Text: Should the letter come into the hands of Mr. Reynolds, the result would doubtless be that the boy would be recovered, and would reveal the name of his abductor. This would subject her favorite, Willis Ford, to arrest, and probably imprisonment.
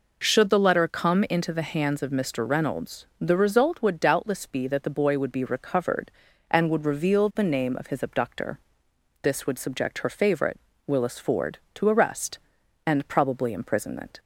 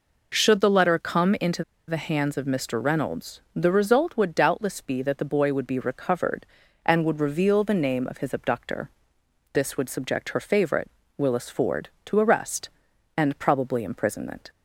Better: first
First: none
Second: pauses between "into" and "the"; slight; at 1.6 s; 0.24 s long

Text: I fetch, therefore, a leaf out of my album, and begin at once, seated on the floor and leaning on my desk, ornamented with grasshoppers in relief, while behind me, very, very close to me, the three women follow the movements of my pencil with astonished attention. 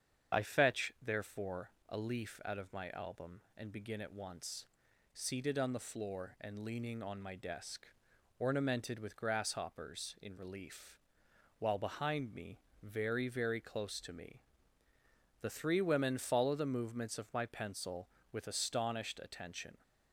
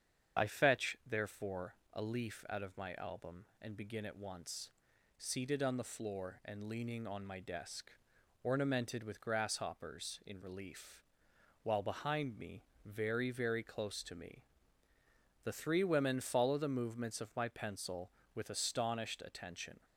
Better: neither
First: starts louder than the rest; strong; until 1.4 s; 8 dB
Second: starts louder than the rest; strong; until 1.4 s; 8 dB

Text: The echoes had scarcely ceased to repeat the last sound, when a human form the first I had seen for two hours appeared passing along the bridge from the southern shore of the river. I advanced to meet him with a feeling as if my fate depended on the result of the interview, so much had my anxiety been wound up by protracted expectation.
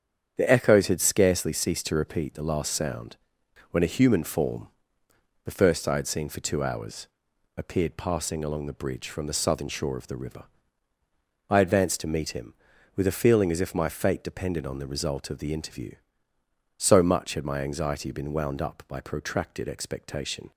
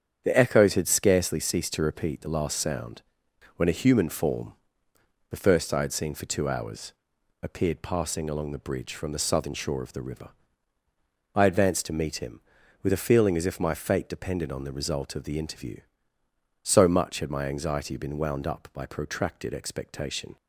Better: neither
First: starts louder than the rest; strong; until 1.3 s; 8 dB // pauses between "form" and "the"; noticeable; at 4.6 s; 0.76 s long // pauses between "hours" and "appeared"; noticeable; at 7.0 s; 0.50 s long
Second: starts louder than the rest; strong; until 1.2 s; 8 dB // pauses between "form" and "the"; noticeable; at 4.5 s; 0.76 s long // pauses between "hours" and "appeared"; noticeable; at 6.9 s; 0.50 s long

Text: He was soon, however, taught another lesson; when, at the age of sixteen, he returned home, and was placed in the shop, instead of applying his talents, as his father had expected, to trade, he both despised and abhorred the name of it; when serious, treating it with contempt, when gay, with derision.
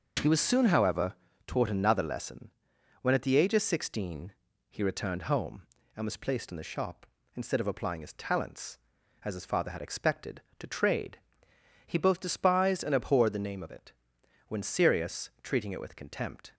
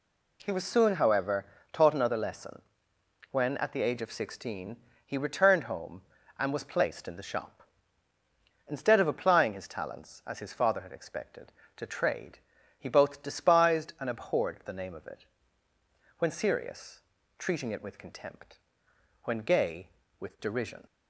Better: second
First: stops before "when gay with derision"; at 16.5 s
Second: none

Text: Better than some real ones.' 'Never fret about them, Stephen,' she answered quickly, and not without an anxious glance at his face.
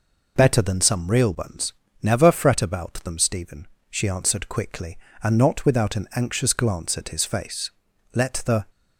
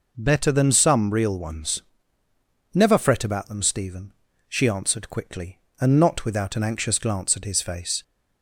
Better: second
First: goes on to say "Let the"; from 8.1 s on; 0.52 s long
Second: none

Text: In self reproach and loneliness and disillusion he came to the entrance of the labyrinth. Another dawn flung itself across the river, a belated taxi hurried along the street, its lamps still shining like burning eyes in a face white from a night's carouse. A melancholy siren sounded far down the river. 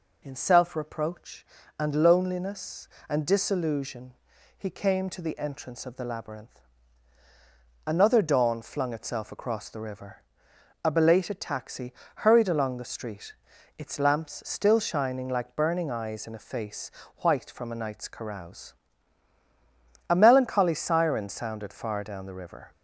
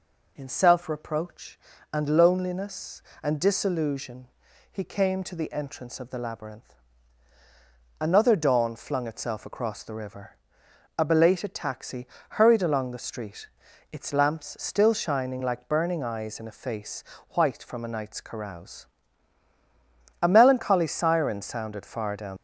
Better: first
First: pauses between "disillusion" and "he"; at 4.1 s; 0.42 s long // pauses between "taxi" and "hurried"; slight; at 11.9 s; 0.26 s long // pauses between "face" and "white"; slight; at 16.9 s; 0.30 s long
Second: pauses between "disillusion" and "he"; at 4.2 s; 0.42 s long // pauses between "taxi" and "hurried"; slight; at 12.0 s; 0.26 s long // pauses between "face" and "white"; slight; at 17.0 s; 0.30 s long // stops before "the river"; at 22.3 s

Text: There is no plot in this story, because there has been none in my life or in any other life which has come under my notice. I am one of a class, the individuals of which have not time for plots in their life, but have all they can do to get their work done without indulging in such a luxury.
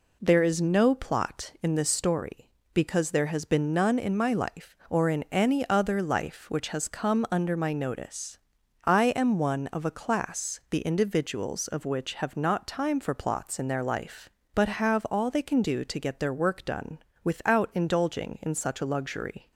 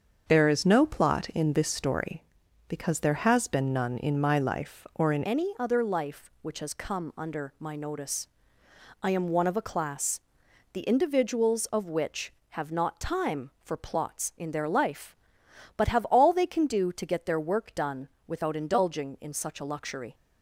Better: first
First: pauses between "done" and "without"; slight; at 16.9 s; 0.26 s long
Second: starts louder than the rest; until 1.2 s; 7 dB // changes voice at "any"; from 5.2 s on; 14.9 s long // pauses between "done" and "without"; slight; at 18.0 s; 0.22 s long

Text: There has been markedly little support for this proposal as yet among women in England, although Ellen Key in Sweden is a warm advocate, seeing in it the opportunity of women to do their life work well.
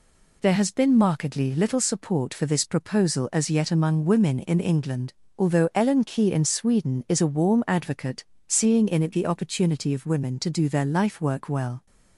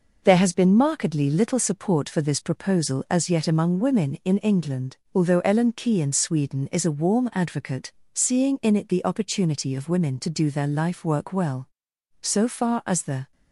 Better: first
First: none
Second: goes on to say "So far as the"; noticeable; from 12.2 s on; 1.1 s long

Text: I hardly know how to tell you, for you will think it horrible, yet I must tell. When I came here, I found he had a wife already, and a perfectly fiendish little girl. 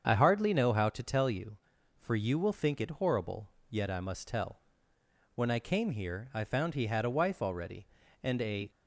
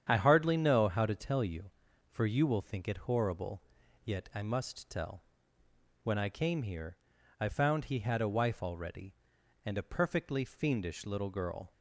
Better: second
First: starts louder than the rest; strong; until 1.0 s; 7.5 dB // stops before "perfectly fiendish little girl"; at 8.6 s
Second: starts louder than the rest; strong; until 1.1 s; 8.5 dB

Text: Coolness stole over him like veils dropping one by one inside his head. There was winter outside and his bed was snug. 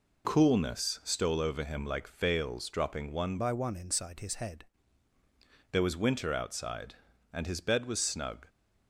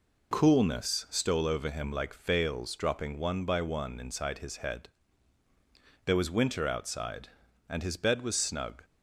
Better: second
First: changes voice from "by" to "head"; from 3.3 to 4.6 s; 1.3 s long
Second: none

